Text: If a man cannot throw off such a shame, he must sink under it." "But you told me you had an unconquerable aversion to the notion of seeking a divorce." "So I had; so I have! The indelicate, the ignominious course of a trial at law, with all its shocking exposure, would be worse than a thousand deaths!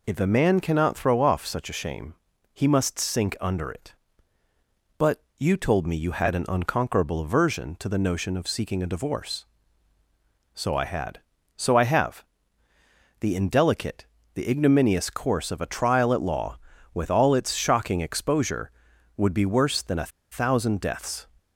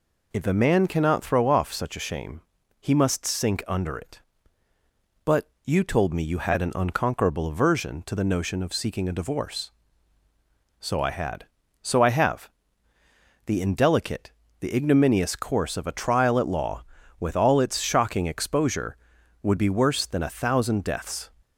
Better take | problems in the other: second | pauses between "But" and "you"; slight; at 5.2 s; 0.16 s long; slight in the second // pauses between "a" and "thousand"; slight; at 20.1 s; 0.21 s long

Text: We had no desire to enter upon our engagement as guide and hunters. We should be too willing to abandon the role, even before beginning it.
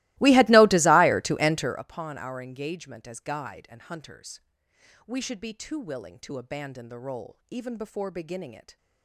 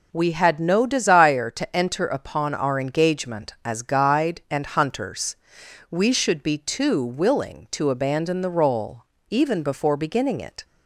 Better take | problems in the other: second | starts louder than the rest; strong; until 1.8 s; 20 dB

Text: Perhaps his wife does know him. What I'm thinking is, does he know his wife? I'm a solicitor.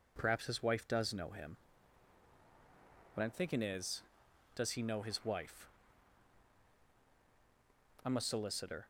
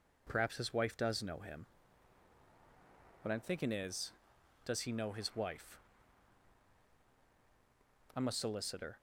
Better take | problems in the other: neither | none

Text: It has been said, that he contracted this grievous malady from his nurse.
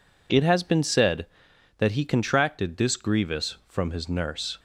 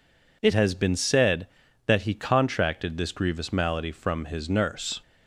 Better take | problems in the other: second | skips "malady"; at 3.6 s

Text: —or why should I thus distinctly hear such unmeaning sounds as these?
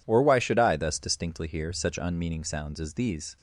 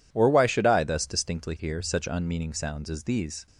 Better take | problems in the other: neither | none

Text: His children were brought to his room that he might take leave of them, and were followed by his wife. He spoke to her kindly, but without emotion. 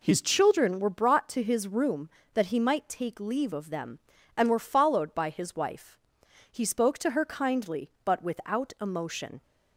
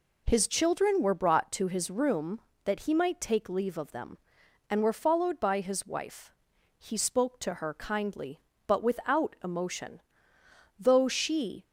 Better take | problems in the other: first | goes on to say "Though she"; noticeable; from 10.7 s on; 0.86 s long

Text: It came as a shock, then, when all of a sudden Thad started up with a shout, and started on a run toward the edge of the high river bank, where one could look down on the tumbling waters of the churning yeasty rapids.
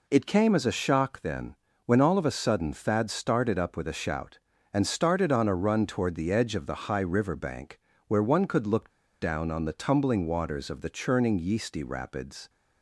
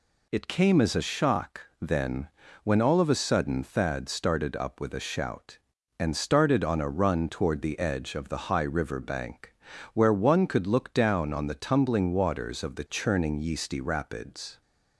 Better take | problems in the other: second | pauses between "look" and "down"; slight; at 8.8 s; 0.31 s long

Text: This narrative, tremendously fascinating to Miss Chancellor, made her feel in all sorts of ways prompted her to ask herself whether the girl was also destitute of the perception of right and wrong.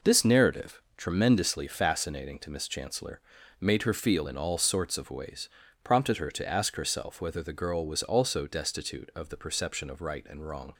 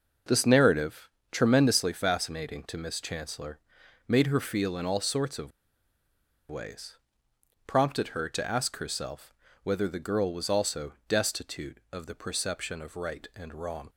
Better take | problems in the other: first | pauses between "of" and "ways"; at 5.5 s; 1.0 s long // pauses between "ways" and "prompted"; noticeable; at 6.9 s; 0.68 s long; slight in the first // pauses between "herself" and "whether"; slight; at 9.3 s; 0.30 s long

